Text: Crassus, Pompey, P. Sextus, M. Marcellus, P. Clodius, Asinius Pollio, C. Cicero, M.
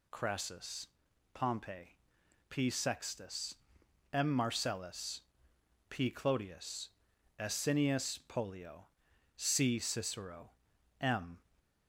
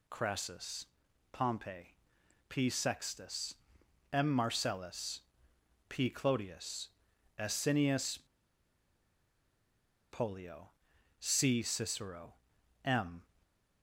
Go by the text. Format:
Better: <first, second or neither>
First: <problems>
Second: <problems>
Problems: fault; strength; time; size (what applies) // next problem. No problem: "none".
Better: first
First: none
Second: pauses between "Asinius" and "Pollio"; strong; at 8.1 s; 1.9 s long